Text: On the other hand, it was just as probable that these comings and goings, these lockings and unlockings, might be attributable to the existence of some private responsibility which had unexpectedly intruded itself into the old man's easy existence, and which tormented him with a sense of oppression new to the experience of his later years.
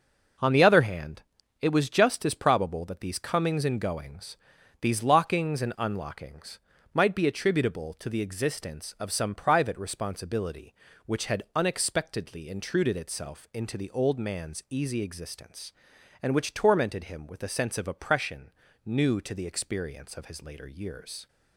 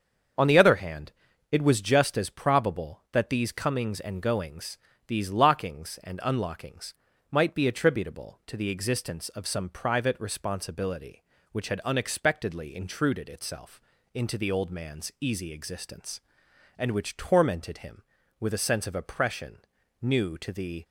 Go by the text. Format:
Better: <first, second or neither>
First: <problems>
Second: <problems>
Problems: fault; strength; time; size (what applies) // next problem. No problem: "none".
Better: first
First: pauses between "oppression" and "new"; slight; at 18.5 s; 0.34 s long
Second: starts louder than the rest; until 1.7 s; 7 dB // pauses between "itself" and "into"; slight; at 13.8 s; 0.32 s long // pauses between "oppression" and "new"; at 19.5 s; 0.42 s long // stops before "experience of his later years"; at 20.8 s